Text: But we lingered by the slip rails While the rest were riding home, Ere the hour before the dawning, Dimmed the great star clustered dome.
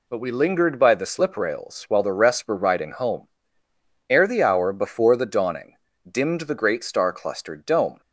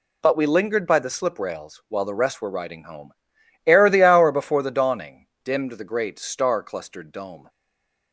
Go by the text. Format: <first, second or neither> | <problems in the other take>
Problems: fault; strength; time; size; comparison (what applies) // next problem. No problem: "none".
first | stays silent after the last word; slight; from 7.4 s on; 0.7 s long